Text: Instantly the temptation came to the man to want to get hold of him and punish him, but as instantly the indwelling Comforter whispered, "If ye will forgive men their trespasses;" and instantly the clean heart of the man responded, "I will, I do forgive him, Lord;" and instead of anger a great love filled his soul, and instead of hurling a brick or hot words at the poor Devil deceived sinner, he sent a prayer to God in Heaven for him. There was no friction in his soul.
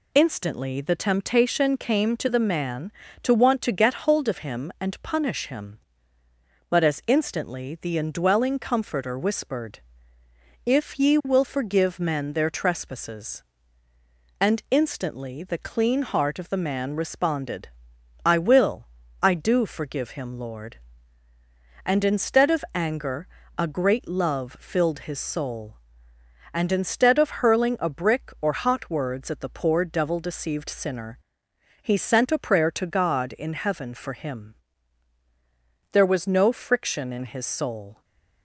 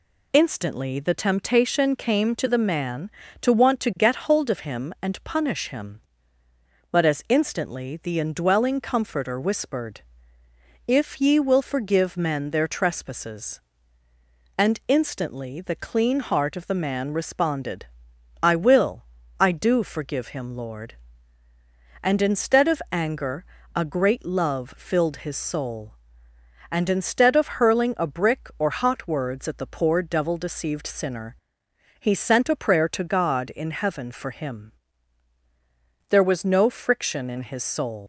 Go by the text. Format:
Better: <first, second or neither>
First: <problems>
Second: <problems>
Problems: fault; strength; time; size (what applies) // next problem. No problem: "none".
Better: first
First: pauses between "anger" and "a"; slight; at 23.2 s; 0.32 s long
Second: pauses between "anger" and "a"; slight; at 23.4 s; 0.32 s long // leaves "soul" unfinished; at 38.0 s; 145 ms